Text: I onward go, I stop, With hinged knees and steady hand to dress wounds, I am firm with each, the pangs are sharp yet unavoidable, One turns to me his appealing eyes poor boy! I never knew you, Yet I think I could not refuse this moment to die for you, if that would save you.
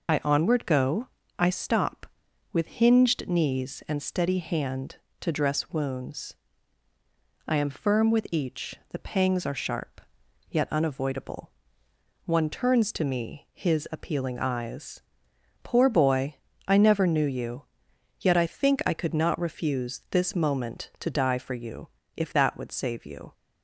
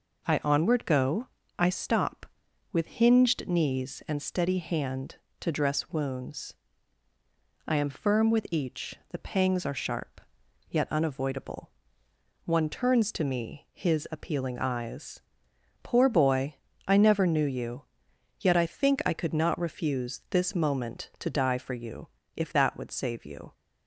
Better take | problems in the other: second | loses the start of "I"; at 0.0 s; 40 ms // pauses between "sharp" and "yet"; noticeable; at 10.0 s; 0.50 s long; noticeable in the second // pauses between "eyes" and "poor"; noticeable; at 15.0 s; 0.62 s long; noticeable in the second

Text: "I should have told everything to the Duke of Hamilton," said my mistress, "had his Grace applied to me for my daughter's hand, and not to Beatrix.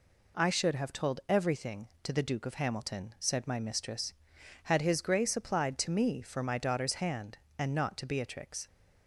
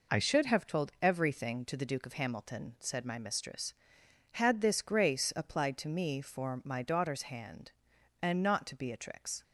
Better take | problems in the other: first | says "this" for "his"; at 4.6 s

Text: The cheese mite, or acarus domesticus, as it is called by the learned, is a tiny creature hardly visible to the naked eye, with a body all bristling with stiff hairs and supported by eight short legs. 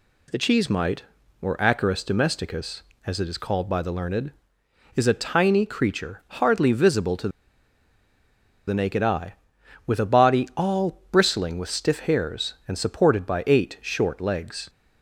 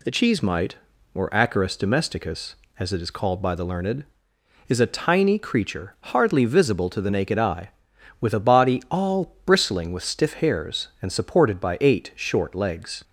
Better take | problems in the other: second | pauses between "to" and "the"; strong; at 7.2 s; 1.3 s long

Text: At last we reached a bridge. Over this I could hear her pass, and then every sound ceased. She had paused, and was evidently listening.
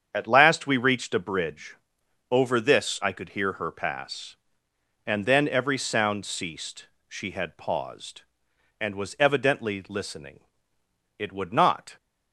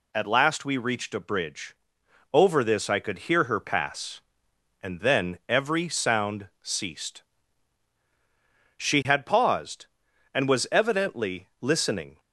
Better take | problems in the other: second | starts louder than the rest; strong; until 1.1 s; 7.5 dB // goes on to say "It would not"; noticeable; from 11.1 s on; 0.80 s long

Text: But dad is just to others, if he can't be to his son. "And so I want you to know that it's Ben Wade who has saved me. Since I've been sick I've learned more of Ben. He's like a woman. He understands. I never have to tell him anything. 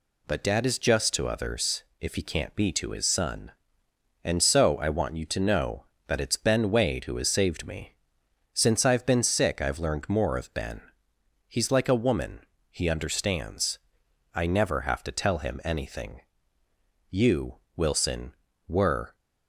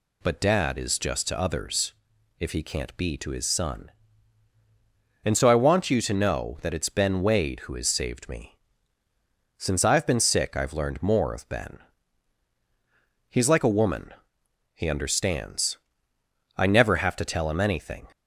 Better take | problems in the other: second | goes on to say "You Wilson were"; strong; from 17.1 s on; 2.0 s long

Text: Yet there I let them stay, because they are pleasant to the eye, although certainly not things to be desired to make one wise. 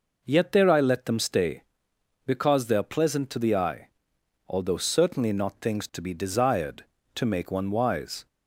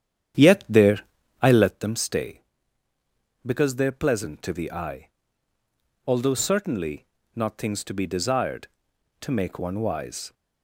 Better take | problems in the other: first | starts louder than the rest; strong; until 1.8 s; 9.5 dB // pauses between "there" and "I"; at 1.0 s; 0.38 s long // pauses between "certainly" and "not"; slight; at 7.0 s; 0.30 s long

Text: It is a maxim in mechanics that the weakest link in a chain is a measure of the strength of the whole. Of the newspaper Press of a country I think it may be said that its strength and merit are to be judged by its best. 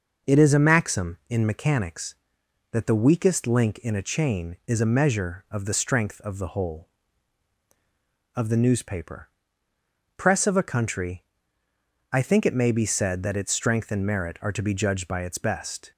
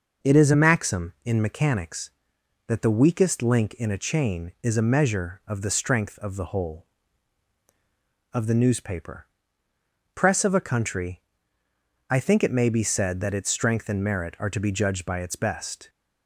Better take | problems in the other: neither | pauses between "newspaper" and "Press"; noticeable; the same in both // pauses between "country" and "I"; noticeable; the same in both

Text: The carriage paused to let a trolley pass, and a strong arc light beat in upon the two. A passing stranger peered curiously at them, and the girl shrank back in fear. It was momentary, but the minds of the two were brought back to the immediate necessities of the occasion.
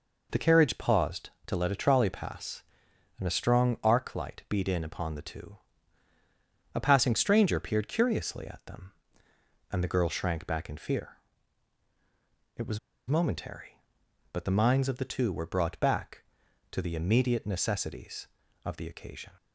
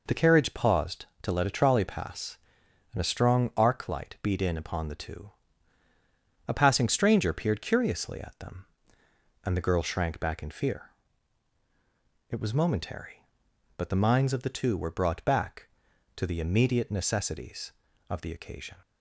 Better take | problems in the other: second | pauses between "was" and "momentary"; slight; at 12.7 s; 0.28 s long

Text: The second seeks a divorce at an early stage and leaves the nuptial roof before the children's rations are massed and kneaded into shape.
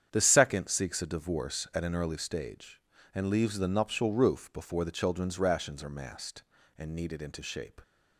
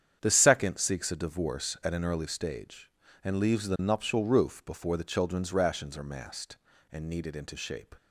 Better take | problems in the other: neither | starts louder than the rest; strong; the same in both

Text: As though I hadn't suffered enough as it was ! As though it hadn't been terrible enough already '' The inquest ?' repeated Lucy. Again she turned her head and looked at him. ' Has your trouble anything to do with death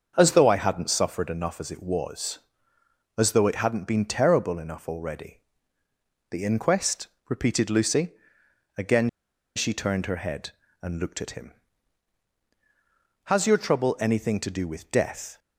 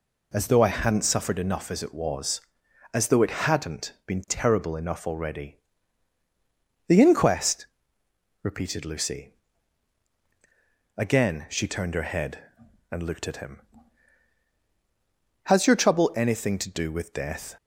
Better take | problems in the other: second | starts louder than the rest; until 1.1 s; 7 dB // pauses between "Again" and "she"; noticeable; at 9.0 s; 0.47 s long

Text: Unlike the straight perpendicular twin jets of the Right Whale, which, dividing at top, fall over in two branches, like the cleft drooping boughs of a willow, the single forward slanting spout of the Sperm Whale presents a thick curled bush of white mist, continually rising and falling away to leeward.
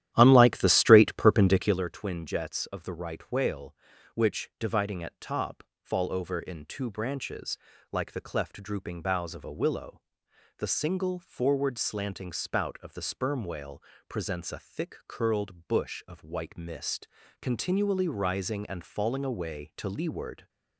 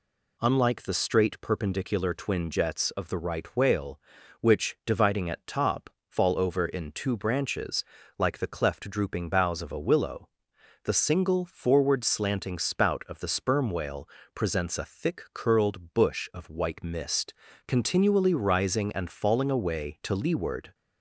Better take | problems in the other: second | starts louder than the rest; strong; until 1.9 s; 12 dB // pauses between "Whale" and "presents"; slight; at 13.8 s; 0.26 s long; slight in the second

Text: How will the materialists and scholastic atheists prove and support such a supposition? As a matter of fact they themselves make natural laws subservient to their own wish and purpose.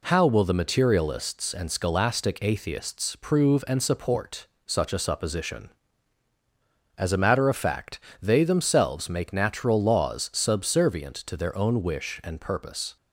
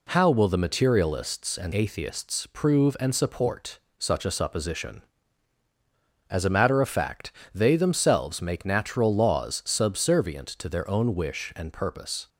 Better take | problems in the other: first | skips "scholastic"; at 1.7 s // pauses between "support" and "such"; slight; at 3.8 s; 0.18 s long; slight in the first // pauses between "fact" and "they"; slight; at 7.3 s; 0.20 s long; slight in the first

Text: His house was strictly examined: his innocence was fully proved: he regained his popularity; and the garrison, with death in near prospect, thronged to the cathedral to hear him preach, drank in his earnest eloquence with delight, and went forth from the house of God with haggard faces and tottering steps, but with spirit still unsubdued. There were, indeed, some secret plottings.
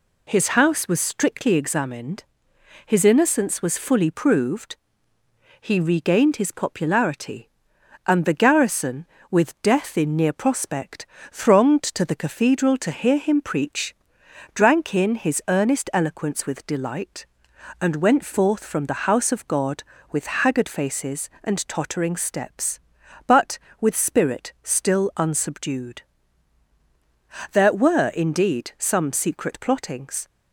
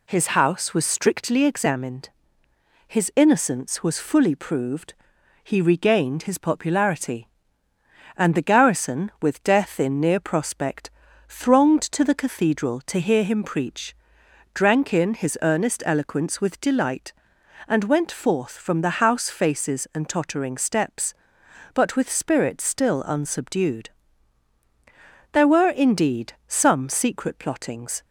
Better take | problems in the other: first | skips "of God with haggard"; at 19.2 s

